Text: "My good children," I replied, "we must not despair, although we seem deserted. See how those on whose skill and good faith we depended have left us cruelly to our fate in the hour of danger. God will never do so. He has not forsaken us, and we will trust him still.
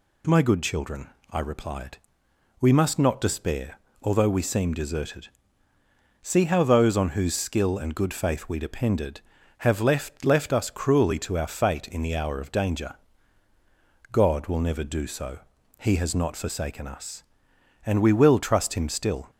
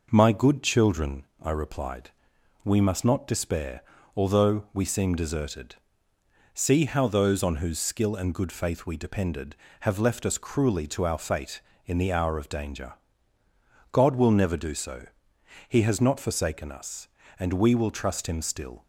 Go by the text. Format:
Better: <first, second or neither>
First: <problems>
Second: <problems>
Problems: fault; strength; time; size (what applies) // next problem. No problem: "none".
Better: second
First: says "left" twice; at 10.2 s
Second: none